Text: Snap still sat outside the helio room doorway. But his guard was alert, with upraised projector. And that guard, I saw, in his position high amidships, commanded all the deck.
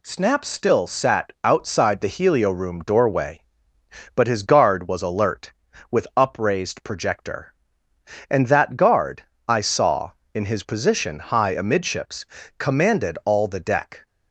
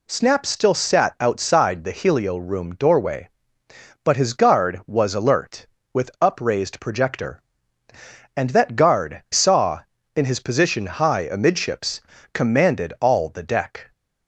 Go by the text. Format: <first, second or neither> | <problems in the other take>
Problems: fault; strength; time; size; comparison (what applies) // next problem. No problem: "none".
first | skips "I"; at 9.2 s